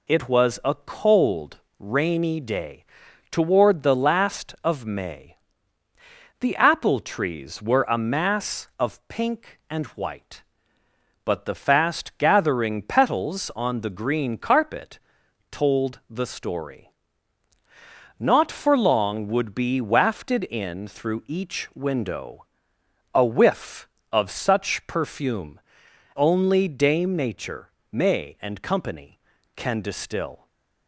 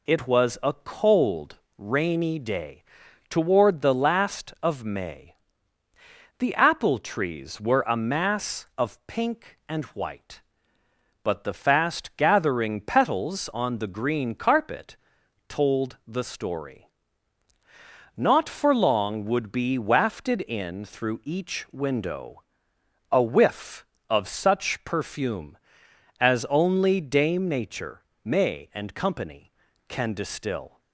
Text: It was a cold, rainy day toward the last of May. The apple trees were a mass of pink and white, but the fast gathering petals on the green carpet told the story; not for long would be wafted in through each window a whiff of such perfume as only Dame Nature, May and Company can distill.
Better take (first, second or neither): second